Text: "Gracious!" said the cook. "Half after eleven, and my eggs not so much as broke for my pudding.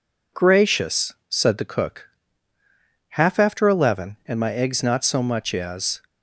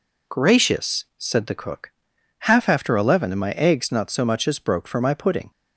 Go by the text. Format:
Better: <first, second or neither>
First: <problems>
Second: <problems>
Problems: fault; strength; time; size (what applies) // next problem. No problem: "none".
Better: second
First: stops before "broke for my pudding"; at 6.0 s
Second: none